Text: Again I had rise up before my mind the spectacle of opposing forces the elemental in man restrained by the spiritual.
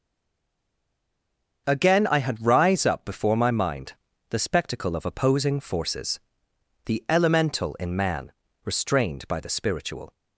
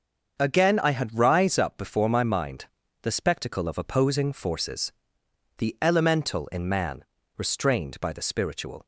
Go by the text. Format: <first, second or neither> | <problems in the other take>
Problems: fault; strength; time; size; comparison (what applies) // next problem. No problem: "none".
second | stays silent before the first word; noticeable; until 1.6 s; 1.6 s long // starts louder than the rest; until 2.6 s; 6.5 dB; also in the second // pauses between "mind" and "the"; at 3.9 s; 0.38 s long; also in the second // pauses between "forces" and "the"; noticeable; at 6.1 s; 0.68 s long; noticeable in the second // pauses between "man" and "restrained"; slight; at 8.3 s; 0.32 s long; slight in the second